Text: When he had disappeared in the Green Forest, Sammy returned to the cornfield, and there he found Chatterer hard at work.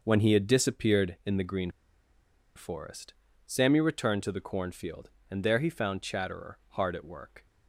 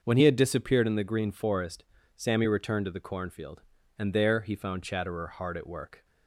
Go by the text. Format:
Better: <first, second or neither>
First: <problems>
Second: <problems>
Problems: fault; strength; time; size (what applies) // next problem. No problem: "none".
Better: second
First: starts louder than the rest; noticeable; until 1.0 s; 6 dB // pauses between "Green" and "Forest"; noticeable; at 1.6 s; 0.86 s long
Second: starts louder than the rest; until 1.0 s; 6 dB